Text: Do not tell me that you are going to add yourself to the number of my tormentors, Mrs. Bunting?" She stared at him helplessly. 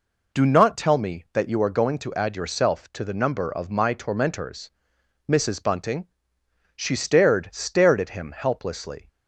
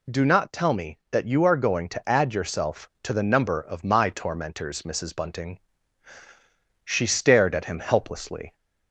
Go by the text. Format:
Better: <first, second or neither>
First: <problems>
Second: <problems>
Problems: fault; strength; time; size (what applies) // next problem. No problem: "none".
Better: second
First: says "stared" twice; at 7.5 s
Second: none